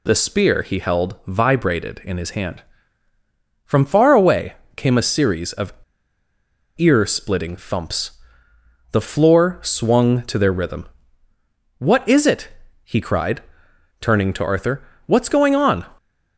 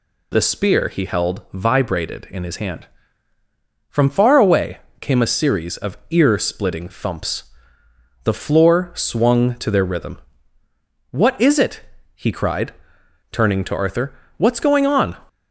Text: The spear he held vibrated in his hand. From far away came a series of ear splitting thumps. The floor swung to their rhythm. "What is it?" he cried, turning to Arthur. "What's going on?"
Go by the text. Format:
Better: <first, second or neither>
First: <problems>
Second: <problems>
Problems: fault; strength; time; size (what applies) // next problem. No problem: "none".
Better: second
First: pauses between "away" and "came"; slight; at 4.5 s; 0.24 s long // pauses between "of" and "ear"; at 5.7 s; 1.0 s long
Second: pauses between "away" and "came"; slight; at 4.7 s; 0.24 s long